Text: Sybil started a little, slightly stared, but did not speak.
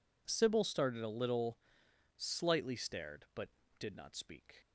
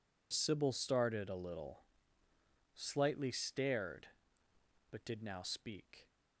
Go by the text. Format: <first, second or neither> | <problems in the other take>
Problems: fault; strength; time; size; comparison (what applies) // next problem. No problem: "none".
first | says "now" for "not"; at 5.2 s